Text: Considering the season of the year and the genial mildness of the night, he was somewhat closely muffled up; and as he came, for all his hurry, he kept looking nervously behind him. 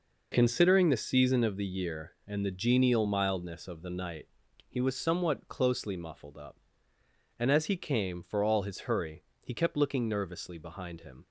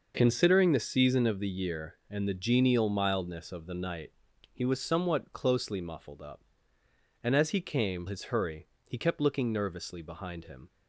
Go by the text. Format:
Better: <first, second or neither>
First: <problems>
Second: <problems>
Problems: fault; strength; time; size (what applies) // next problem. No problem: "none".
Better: first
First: none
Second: skips "for all"; at 8.0 s